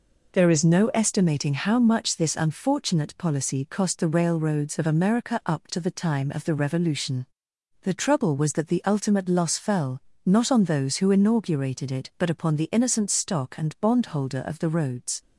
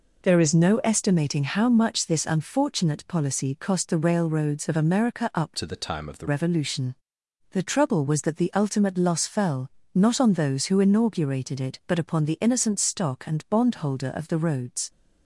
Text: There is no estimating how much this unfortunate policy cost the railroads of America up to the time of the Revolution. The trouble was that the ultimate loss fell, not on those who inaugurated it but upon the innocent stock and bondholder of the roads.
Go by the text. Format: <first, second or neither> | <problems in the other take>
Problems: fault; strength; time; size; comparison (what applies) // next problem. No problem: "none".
first | changes voice from "to" to "the"; from 5.5 to 6.2 s; 0.7 s long